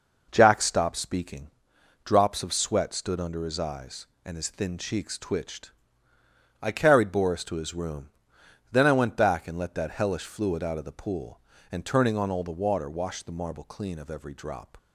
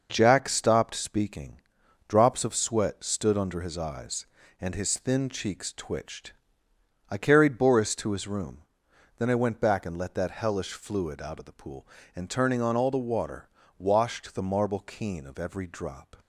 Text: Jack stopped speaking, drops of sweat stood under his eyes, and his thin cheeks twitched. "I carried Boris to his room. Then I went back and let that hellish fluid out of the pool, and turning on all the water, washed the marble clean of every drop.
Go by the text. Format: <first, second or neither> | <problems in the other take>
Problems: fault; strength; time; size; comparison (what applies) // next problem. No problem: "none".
first | says "keen" for "clean"; at 14.8 s